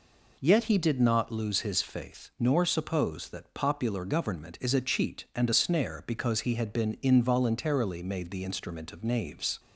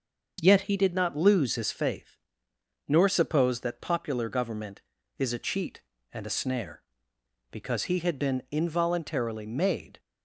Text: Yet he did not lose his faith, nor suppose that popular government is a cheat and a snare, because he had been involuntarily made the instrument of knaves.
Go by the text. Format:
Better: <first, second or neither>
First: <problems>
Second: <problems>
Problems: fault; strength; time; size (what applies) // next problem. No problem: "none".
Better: first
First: none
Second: starts louder than the rest; until 1.4 s; 6.5 dB // stops before "the instrument of knaves"; at 9.9 s